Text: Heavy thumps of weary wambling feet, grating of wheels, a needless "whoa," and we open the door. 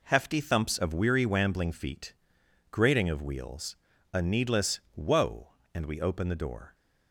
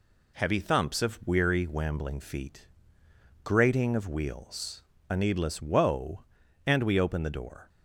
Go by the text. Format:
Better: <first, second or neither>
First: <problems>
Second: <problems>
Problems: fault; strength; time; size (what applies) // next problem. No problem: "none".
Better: second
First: says "Hefty" for "Heavy"; at 0.0 s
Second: none